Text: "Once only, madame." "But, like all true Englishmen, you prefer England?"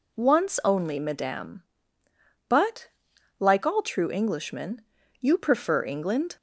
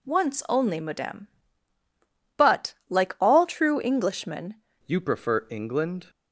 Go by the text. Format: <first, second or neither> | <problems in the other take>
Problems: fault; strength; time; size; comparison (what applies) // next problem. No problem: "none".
first | changes voice at "you"; from 4.8 s on; 1.2 s long